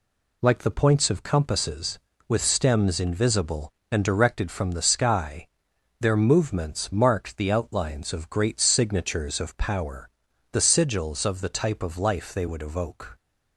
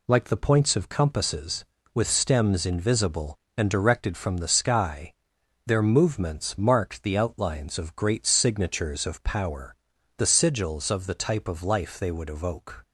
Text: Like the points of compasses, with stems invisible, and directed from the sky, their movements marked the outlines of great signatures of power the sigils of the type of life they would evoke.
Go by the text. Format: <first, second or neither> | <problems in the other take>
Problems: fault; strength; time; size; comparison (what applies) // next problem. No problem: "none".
neither | pauses between "power" and "the"; the same in both